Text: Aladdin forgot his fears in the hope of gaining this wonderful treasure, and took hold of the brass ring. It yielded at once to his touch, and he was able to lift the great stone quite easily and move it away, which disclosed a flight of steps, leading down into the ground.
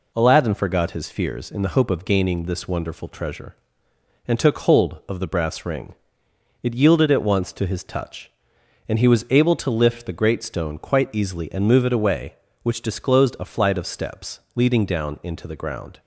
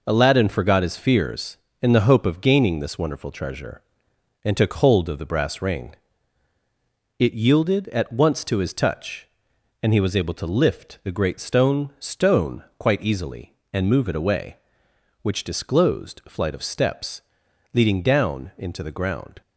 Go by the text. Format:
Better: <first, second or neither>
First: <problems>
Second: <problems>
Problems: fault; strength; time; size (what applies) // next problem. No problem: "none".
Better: first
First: none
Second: says "stone" twice; at 11.9 s